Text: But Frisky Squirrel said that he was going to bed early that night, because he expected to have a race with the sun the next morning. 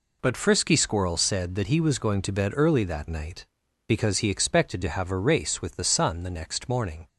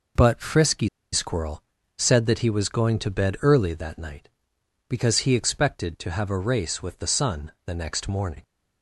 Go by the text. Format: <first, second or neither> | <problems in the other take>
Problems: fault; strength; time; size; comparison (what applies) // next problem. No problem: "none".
first | pauses between "Frisky" and "Squirrel"; slight; at 0.8 s; 0.24 s long // pauses between "Squirrel" and "said"; slight; at 1.6 s; 0.36 s long